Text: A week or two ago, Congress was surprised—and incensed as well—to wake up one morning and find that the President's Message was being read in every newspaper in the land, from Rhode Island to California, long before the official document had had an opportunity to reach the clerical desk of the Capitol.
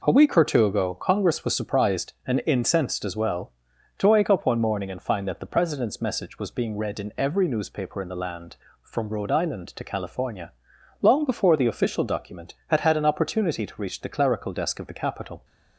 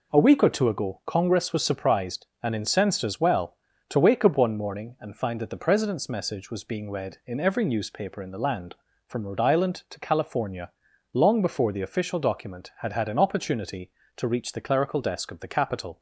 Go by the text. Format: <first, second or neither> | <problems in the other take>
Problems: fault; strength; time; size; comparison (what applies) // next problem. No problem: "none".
neither | none